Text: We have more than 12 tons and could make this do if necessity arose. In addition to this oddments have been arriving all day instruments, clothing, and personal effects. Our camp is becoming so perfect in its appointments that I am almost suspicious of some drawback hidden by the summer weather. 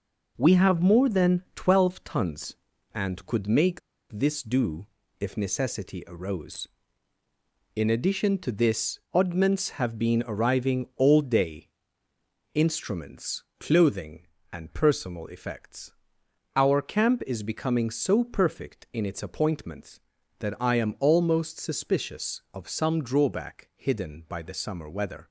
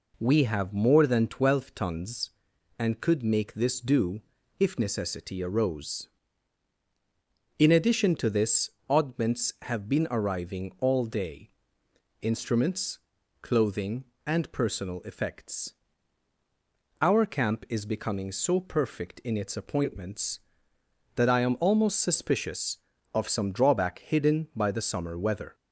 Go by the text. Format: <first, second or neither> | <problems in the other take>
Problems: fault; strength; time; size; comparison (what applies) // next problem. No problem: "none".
second | pauses between "make" and "this"; slight; at 3.8 s; 0.31 s long // pauses between "do" and "if"; slight; at 4.8 s; 0.32 s long; also in the second // pauses between "this" and "oddments"; slight; at 8.9 s; 0.16 s long; slight in the second // pauses between "day" and "instruments"; noticeable; at 11.6 s; 0.86 s long; noticeable in the second